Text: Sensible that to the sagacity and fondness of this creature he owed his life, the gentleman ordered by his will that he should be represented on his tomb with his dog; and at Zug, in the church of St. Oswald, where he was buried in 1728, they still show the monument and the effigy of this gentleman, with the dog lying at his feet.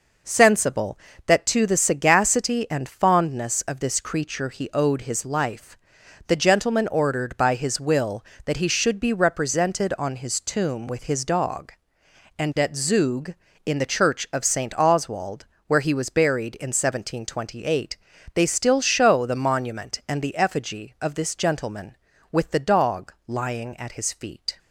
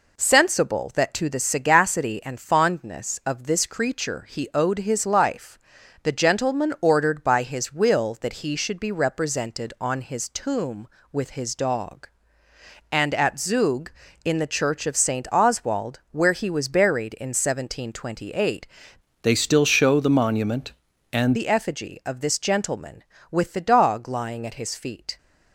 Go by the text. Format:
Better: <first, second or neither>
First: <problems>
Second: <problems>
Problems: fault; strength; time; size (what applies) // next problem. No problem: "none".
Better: first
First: none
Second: changes voice from "they" to "and"; from 19.2 to 21.3 s; 2.1 s long